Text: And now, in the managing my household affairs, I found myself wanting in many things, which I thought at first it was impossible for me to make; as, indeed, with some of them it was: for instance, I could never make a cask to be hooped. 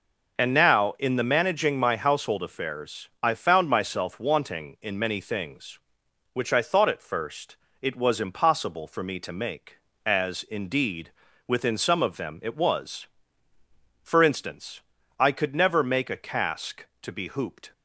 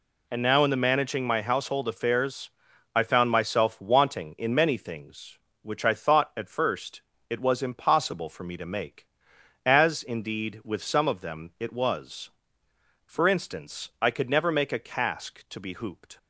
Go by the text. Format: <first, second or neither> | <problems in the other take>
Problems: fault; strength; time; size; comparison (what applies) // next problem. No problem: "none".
second | pauses between "first" and "it"; slight; at 7.5 s; 0.24 s long; slight in the second // says "within" for "with"; at 11.4 s